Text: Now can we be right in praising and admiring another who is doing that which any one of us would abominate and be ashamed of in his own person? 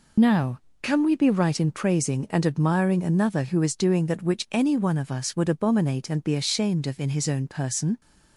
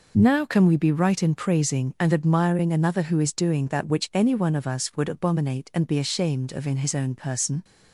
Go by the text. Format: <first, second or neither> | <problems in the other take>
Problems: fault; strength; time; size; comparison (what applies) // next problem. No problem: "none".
second | loses the start of "Now"; at 0.1 s; 55 ms